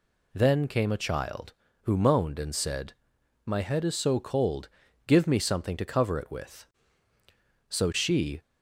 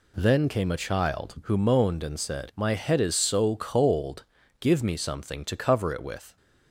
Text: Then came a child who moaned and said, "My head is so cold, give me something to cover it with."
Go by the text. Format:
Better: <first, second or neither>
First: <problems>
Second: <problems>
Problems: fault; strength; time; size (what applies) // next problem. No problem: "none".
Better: second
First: goes on to say "So she"; noticeable; from 7.6 s on; 0.73 s long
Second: none